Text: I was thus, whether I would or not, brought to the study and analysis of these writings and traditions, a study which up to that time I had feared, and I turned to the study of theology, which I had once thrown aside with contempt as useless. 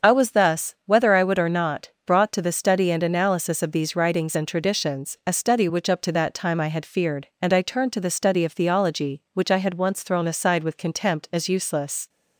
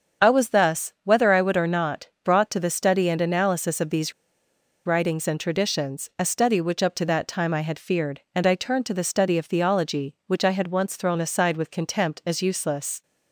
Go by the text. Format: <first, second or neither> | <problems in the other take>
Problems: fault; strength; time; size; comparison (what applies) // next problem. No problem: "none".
first | starts louder than the rest; until 1.3 s; 7 dB; also in the first // pauses between "these" and "writings"; noticeable; at 4.1 s; 0.73 s long